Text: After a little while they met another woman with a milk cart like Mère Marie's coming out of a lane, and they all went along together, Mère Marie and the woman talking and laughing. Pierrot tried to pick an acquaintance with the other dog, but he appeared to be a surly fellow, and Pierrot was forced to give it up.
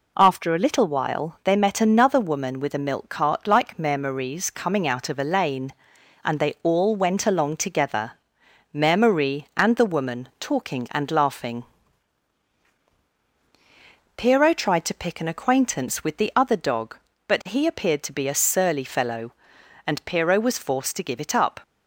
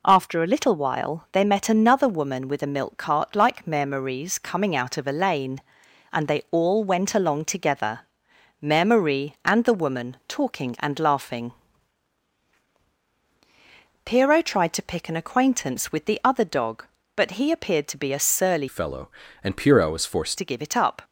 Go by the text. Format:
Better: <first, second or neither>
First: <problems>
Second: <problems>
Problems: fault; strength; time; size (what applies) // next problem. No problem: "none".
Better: first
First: none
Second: changes voice from "fellow" to "forced"; from 18.6 to 20.3 s; 1.7 s long